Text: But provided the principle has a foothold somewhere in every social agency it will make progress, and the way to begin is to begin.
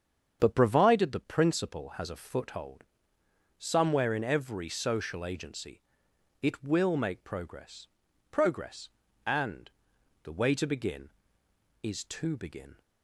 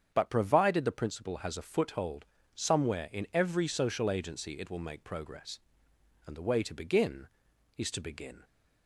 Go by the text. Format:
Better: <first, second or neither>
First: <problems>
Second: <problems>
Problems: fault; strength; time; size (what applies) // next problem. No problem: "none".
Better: second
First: starts louder than the rest; strong; until 1.4 s; 8 dB // pauses between "foothold" and "somewhere"; noticeable; at 2.8 s; 0.76 s long // pauses between "agency" and "it"; noticeable; at 5.8 s; 0.58 s long // says "progress" twice; at 8.3 s // pauses between "and" and "the"; noticeable; at 9.6 s; 0.54 s long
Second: starts louder than the rest; strong; until 1.1 s; 8 dB // pauses between "foothold" and "somewhere"; slight; at 2.2 s; 0.28 s long